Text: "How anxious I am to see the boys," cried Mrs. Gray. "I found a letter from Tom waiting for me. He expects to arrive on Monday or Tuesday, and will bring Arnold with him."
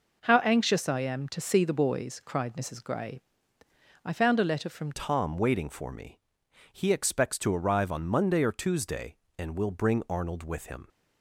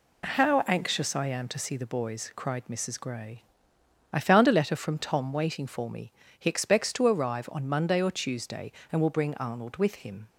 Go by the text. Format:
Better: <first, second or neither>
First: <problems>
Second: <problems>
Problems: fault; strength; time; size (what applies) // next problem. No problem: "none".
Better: second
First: changes voice at "Tom"; from 4.9 s on; 5.9 s long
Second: none